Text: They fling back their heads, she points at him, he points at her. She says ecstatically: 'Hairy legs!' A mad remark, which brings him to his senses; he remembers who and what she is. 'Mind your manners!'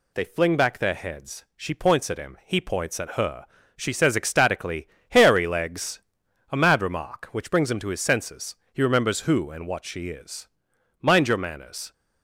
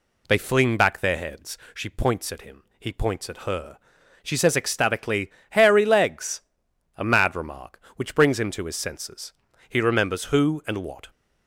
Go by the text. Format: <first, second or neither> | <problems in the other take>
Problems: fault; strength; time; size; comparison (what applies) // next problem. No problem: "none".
first | stops before "she is Mind your manners"; at 11.0 s